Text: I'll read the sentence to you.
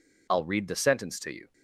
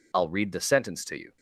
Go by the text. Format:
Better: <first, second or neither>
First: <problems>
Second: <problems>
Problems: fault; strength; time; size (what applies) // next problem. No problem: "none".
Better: neither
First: none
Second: none